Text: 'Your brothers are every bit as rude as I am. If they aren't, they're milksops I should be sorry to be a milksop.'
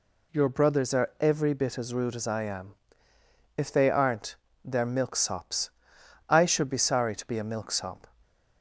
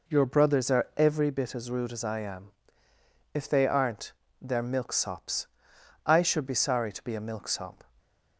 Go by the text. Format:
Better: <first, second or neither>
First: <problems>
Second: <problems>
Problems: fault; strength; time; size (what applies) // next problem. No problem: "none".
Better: first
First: pauses between "milksops" and "I"; noticeable; at 5.6 s; 0.60 s long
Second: starts louder than the rest; noticeable; until 1.3 s; 4 dB // pauses between "milksops" and "I"; noticeable; at 5.4 s; 0.60 s long